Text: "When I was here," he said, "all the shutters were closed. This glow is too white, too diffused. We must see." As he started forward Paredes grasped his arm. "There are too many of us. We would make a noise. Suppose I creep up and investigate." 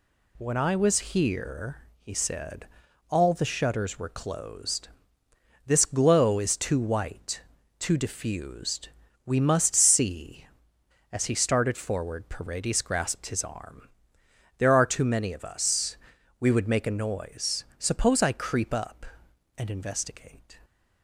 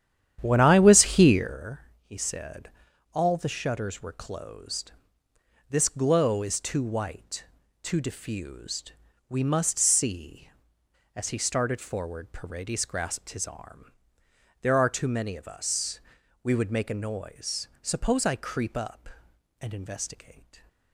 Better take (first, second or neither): first